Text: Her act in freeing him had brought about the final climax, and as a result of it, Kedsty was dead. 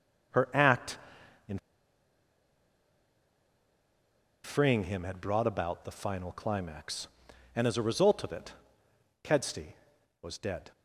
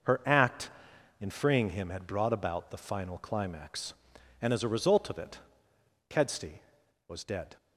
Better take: second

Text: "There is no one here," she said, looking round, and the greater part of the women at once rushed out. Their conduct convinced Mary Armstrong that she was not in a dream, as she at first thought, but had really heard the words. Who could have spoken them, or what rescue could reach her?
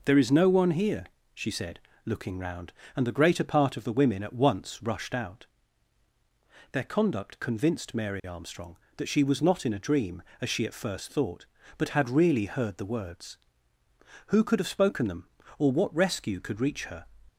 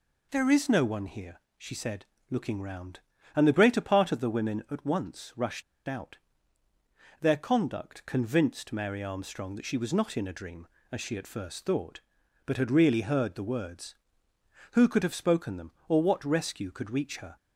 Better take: first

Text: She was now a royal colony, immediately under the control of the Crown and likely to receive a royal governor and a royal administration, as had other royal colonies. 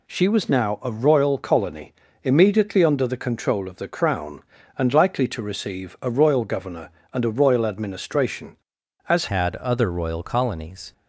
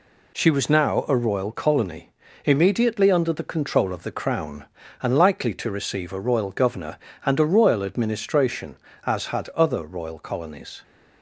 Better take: second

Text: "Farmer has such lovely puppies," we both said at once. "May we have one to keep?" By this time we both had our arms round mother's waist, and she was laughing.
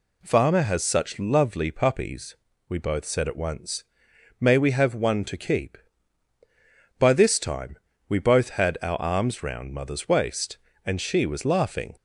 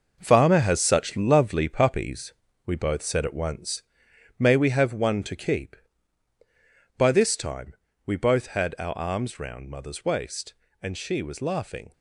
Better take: first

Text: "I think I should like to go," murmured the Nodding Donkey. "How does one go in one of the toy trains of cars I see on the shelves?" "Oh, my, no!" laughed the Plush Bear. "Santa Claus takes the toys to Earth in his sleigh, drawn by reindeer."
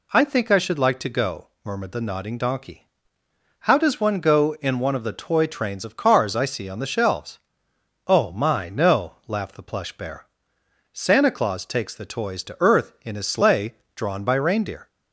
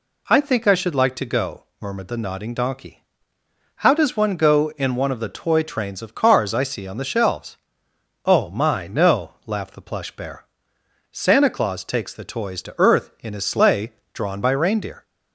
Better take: neither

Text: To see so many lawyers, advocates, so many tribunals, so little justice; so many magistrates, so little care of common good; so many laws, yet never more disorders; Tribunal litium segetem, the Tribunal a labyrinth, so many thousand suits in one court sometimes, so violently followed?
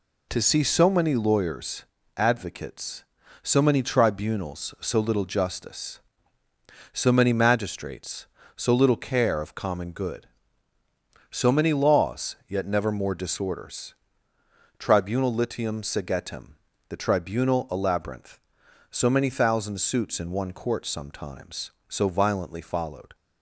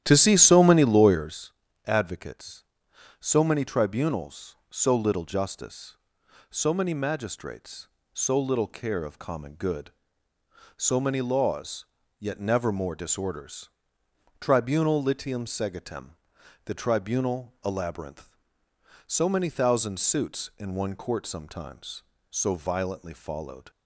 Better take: first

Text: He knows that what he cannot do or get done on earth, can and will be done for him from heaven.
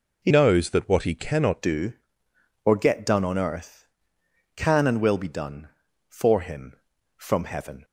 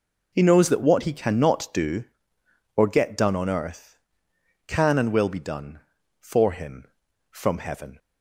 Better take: second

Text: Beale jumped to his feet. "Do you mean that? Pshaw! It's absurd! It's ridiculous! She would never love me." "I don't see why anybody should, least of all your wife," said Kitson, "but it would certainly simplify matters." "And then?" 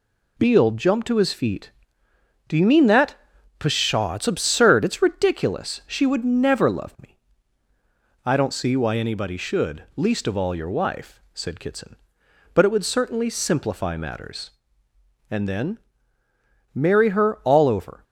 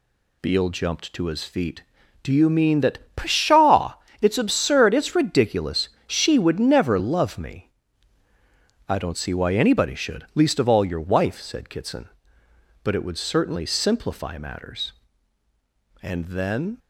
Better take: second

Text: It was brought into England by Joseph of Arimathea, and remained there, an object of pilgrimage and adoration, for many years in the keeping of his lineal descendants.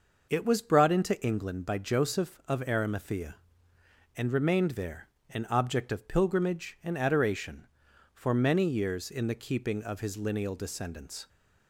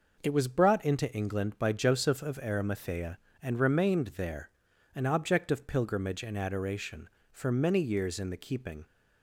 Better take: first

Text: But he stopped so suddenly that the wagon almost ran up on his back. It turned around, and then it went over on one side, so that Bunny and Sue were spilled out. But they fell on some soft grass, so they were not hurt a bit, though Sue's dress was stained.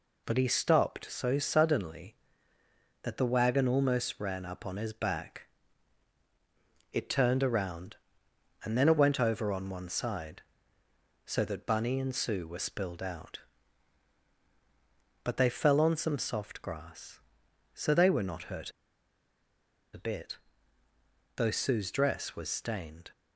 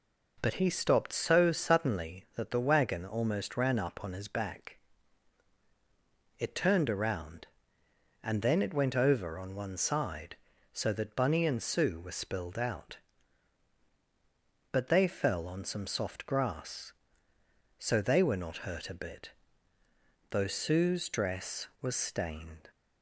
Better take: second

